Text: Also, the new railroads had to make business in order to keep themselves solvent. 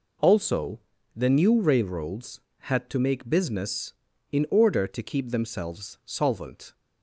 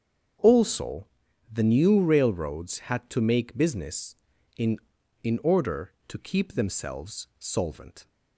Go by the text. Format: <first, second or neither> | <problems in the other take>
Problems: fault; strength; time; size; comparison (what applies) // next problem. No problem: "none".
first | starts louder than the rest; strong; until 1.8 s; 7.5 dB // says "in" twice; at 5.2 s